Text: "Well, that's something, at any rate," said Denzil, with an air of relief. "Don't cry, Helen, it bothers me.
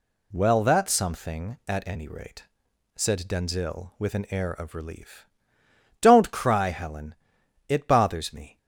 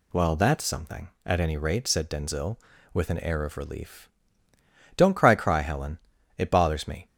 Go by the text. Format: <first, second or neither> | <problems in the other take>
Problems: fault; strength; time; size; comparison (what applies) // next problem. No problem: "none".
first | says "cry" twice; at 5.3 s